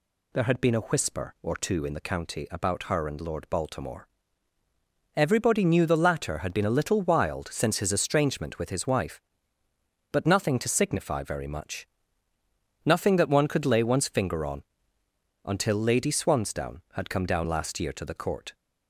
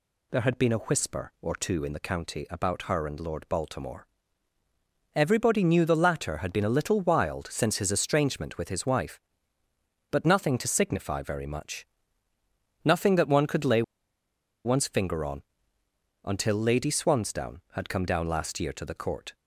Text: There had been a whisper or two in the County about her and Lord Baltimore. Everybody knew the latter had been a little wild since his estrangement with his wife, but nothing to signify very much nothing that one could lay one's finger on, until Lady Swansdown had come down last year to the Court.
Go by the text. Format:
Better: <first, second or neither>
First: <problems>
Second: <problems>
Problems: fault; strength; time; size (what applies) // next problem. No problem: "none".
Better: first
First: pauses between "much" and "nothing"; noticeable; at 11.8 s; 0.96 s long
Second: pauses between "much" and "nothing"; noticeable; at 11.8 s; 0.96 s long // pauses between "lay" and "one's"; noticeable; at 13.8 s; 0.83 s long